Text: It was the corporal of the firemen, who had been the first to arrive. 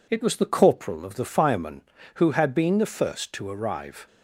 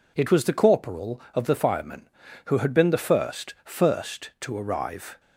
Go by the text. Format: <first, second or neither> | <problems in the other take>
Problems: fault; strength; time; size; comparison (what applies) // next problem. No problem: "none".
first | says "first" twice; at 3.6 s